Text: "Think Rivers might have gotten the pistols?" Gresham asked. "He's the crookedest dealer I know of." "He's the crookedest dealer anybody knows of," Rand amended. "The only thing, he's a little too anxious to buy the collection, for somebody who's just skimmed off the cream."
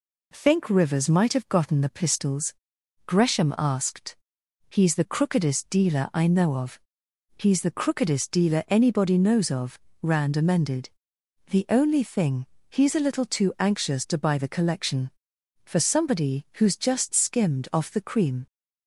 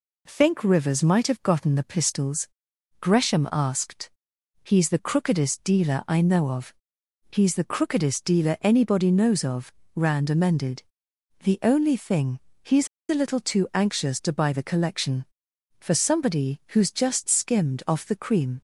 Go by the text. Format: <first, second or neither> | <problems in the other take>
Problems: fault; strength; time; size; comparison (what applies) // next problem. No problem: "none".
first | pauses between "he's" and "a"; slight; at 12.8 s; 0.23 s long